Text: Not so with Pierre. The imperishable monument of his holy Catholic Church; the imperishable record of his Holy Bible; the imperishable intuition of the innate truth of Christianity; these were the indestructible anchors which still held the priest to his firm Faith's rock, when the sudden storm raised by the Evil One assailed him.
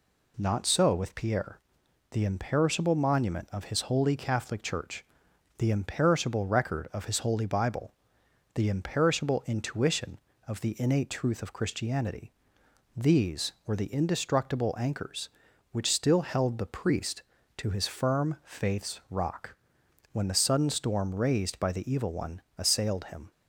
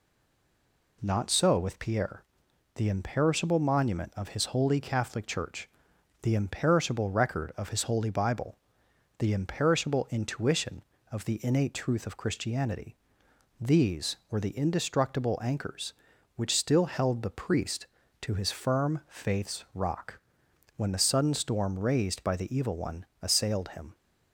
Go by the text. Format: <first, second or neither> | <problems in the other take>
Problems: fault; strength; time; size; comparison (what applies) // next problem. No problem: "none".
first | stays silent before the first word; until 1.0 s; 1.0 s long // pauses between "One" and "assailed"; slight; at 23.0 s; 0.16 s long; slight in the first